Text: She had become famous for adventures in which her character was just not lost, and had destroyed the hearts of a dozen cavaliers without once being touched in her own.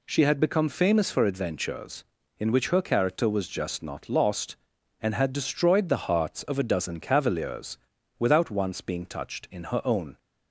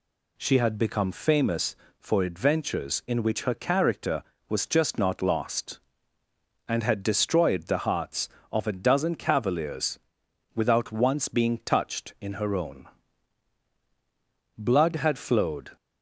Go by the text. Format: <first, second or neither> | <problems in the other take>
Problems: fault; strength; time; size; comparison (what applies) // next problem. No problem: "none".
first | pauses between "cavaliers" and "without"; noticeable; at 9.9 s; 0.56 s long; also in the first // goes on to say "Blood had flowed"; noticeable; from 14.5 s on; 1.1 s long